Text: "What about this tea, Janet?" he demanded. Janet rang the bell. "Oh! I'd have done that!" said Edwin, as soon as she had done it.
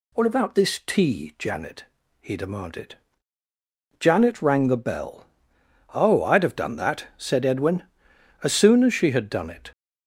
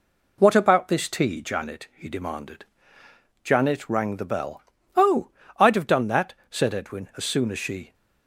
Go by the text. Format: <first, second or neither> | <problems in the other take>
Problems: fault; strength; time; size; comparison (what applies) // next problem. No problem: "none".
first | stops before "had done it"; at 7.9 s